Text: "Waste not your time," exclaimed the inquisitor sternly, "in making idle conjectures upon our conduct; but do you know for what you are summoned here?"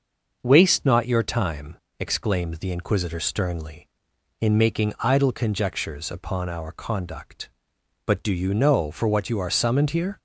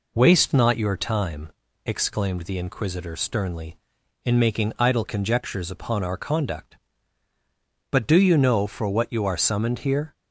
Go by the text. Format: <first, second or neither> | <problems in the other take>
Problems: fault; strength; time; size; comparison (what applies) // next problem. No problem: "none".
neither | none